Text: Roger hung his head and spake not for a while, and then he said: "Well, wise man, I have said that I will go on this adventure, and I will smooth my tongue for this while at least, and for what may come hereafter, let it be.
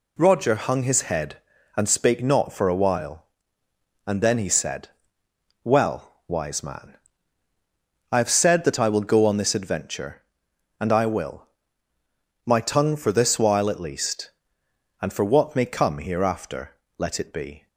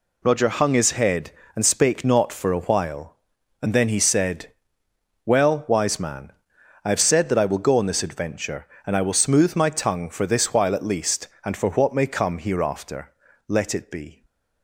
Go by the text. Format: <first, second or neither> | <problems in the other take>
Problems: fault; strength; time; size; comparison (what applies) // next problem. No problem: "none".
second | skips "smooth"; at 11.9 s